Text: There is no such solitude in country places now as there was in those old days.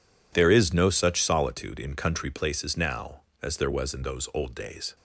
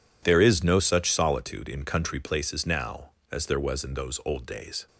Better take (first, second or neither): neither